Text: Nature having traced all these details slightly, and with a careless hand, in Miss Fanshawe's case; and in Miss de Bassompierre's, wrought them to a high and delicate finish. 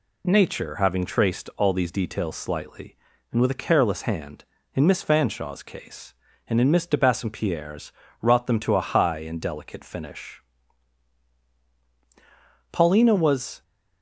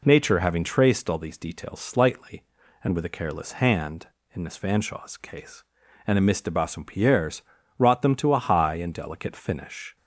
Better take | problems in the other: second | goes on to say "Paulina was"; noticeable; from 12.7 s on; 0.90 s long

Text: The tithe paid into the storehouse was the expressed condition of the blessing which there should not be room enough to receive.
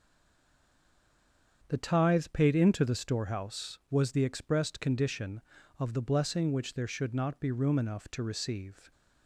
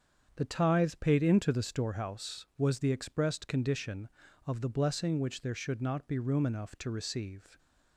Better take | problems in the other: second | stays silent before the first word; noticeable; until 1.6 s; 1.6 s long // starts louder than the rest; strong; until 2.7 s; 7.5 dB; strong in the second

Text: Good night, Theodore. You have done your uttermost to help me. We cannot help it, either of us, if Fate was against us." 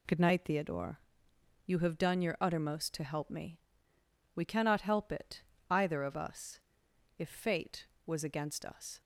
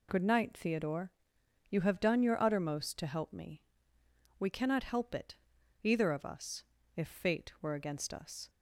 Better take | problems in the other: first | says "were" for "was"; at 7.6 s

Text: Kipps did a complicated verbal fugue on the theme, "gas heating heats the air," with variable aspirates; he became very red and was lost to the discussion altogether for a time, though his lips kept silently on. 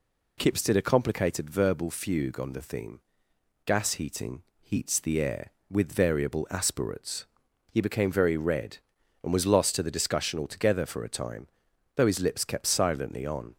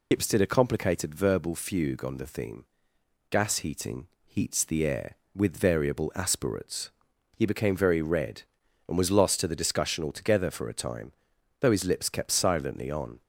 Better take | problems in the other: first | loses the start of "Kipps"; at 0.1 s; 85 ms // pauses between "heating" and "heats"; slight; at 4.0 s; 0.18 s long; slight in the first

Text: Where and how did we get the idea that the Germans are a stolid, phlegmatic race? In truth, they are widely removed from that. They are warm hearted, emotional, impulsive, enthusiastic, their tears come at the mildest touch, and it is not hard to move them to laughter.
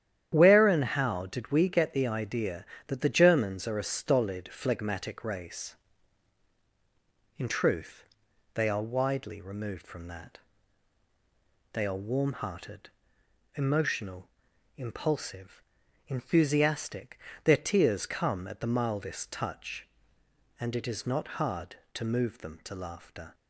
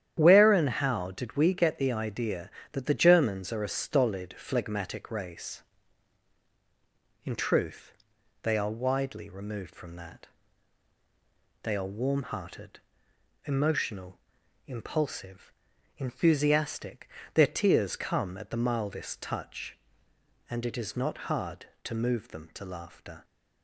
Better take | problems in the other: neither | starts louder than the rest; strong; the same in both

